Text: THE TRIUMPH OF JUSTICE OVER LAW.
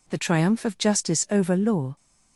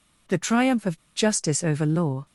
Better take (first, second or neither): first